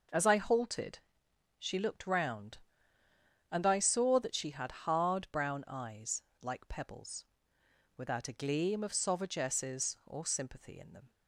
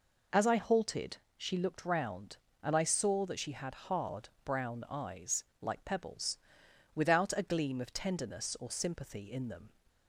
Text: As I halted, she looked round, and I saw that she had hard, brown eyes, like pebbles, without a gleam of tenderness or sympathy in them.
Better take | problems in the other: second | says "sauvagesses" for "tenderness"; at 8.9 s

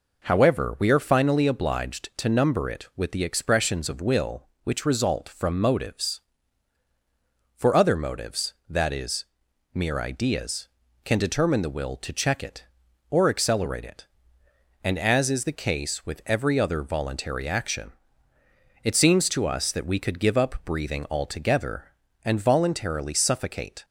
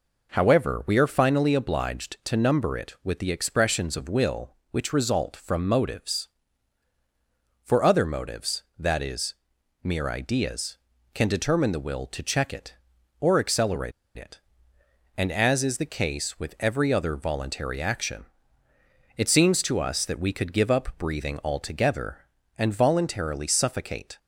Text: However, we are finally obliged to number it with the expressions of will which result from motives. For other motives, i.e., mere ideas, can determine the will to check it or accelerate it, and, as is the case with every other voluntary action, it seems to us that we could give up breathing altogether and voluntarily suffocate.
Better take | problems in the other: first | pauses between "accelerate" and "it"; slight; at 13.9 s; 0.25 s long

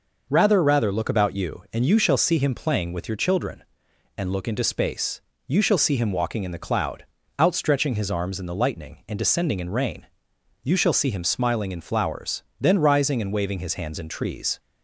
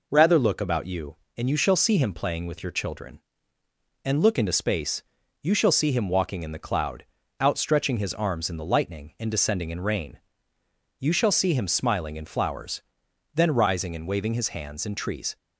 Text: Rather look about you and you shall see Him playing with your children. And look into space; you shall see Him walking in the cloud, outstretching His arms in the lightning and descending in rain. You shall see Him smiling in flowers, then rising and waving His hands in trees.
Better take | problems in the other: second | says "Rather" twice; at 0.6 s

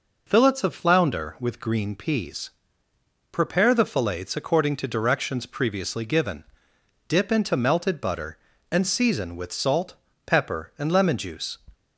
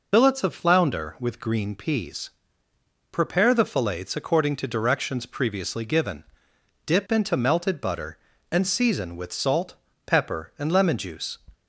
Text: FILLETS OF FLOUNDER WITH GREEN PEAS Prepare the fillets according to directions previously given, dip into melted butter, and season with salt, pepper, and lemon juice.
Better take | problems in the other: first | loses the start of "FILLETS"; at 0.1 s; 55 ms // pauses between "PEAS" and "Prepare"; noticeable; at 2.2 s; 0.82 s long; noticeable in the first

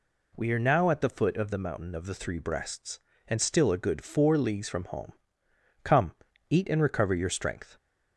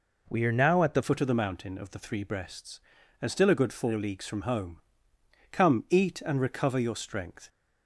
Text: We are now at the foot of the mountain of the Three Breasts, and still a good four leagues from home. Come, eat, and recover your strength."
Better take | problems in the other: first | changes voice at "foot"; from 1.0 s on; 6.4 s long

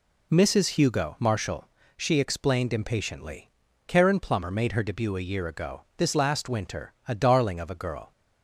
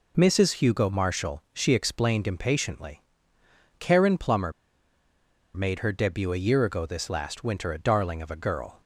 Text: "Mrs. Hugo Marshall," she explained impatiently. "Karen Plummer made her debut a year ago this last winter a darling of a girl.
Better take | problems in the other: first | pauses between "Plummer" and "made"; at 4.4 s; 1.0 s long

